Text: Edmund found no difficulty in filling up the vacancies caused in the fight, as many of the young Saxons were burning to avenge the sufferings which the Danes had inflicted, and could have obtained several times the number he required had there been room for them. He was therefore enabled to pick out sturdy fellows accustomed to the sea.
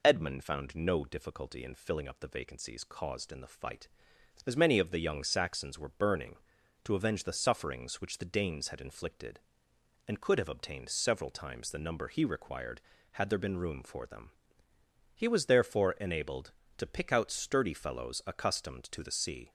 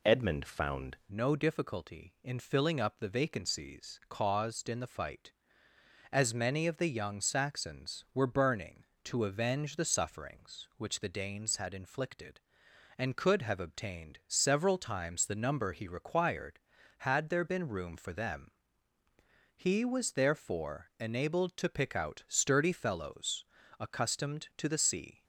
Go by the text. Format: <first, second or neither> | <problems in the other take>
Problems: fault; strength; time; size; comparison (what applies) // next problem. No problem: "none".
first | changes voice at "no"; from 1.1 s on; 24.1 s long // pauses between "fellows" and "accustomed"; slight; at 23.4 s; 0.34 s long